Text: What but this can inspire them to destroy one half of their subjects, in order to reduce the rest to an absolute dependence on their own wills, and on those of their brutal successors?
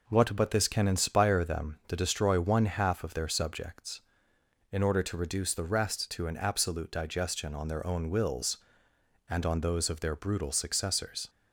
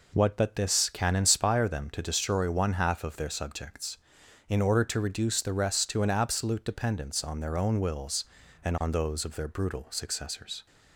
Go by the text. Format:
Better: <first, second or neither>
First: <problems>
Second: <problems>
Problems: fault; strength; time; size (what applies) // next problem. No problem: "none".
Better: second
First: says "digestion" for "dependence"; at 6.9 s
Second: none